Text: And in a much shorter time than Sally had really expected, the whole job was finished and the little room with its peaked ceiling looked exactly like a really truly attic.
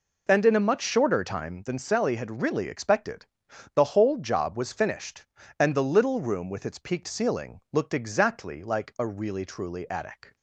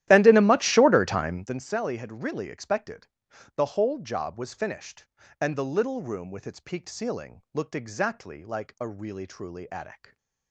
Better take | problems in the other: first | starts louder than the rest; strong; until 1.6 s; 13 dB

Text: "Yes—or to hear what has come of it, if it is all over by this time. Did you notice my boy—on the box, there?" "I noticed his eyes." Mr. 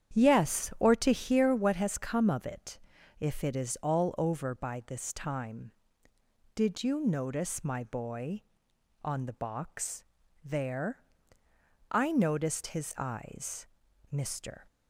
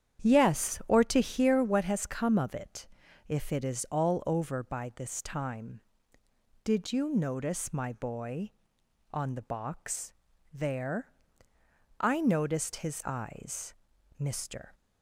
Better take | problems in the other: neither | starts louder than the rest; strong; the same in both

